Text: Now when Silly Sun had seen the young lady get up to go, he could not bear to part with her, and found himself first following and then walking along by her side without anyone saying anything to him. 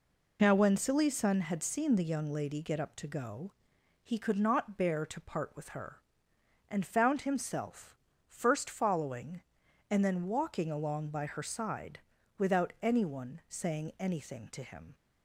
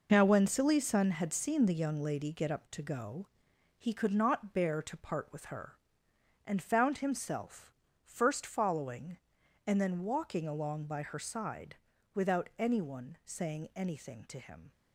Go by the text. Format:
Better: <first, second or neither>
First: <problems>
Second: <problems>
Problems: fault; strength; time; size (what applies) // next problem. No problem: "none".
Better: first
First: pauses between "himself" and "first"; slight; at 7.9 s; 0.32 s long // pauses between "side" and "without"; at 11.9 s; 0.40 s long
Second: gets quieter; strong; throughout; 8 dB // pauses between "himself" and "first"; slight; at 7.7 s; 0.32 s long // pauses between "side" and "without"; at 11.7 s; 0.40 s long